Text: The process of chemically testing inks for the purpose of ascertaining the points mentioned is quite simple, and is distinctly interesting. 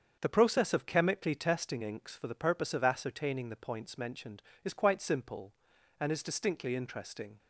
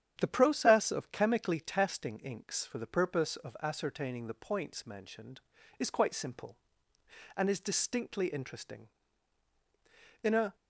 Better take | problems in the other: first | starts louder than the rest; strong; until 1.1 s; 9.5 dB; also in the first // goes on to say "In a"; slight; from 10.2 s on; 0.32 s long

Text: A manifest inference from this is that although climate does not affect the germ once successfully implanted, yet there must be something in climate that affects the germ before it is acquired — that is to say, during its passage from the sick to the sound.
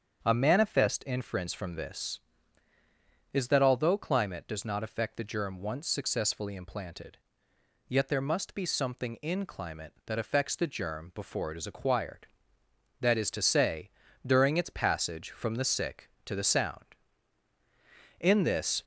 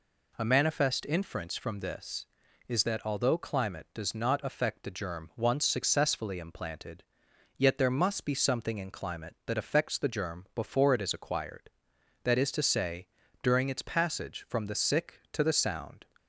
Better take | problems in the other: second | starts louder than the rest; strong; until 1.2 s; 7.5 dB // goes on to say "In this"; noticeable; from 18.1 s on; 0.64 s long

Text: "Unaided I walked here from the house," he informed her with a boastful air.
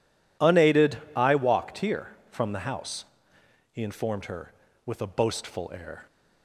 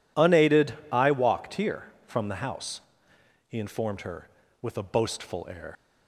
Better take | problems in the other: first | pauses between "Unaided" and "I"; slight; at 0.7 s; 0.18 s long; slight in the first // leaves "air" unfinished; at 5.7 s; 70 ms

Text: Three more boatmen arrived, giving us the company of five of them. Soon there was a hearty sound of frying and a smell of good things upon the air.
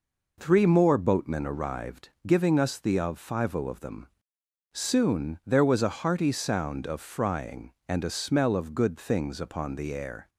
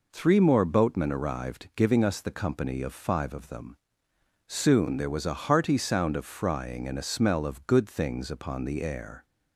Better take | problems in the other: second | skips "company"; at 2.9 s

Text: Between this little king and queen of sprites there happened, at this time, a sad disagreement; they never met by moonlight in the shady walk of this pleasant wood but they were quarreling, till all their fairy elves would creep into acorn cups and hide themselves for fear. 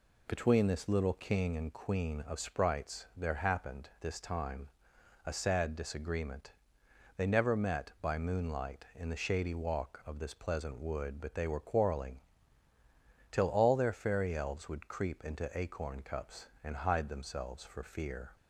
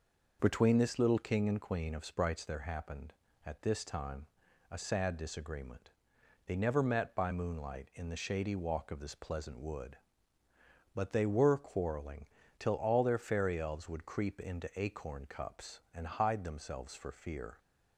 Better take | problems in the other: second | skips "at"; at 3.9 s

